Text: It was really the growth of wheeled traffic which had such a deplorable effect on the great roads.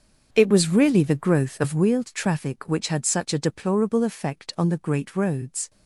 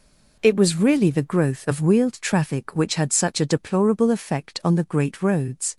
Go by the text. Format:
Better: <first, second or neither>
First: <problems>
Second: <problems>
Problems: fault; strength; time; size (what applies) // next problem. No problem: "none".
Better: second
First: starts louder than the rest; until 1.8 s; 6.5 dB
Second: none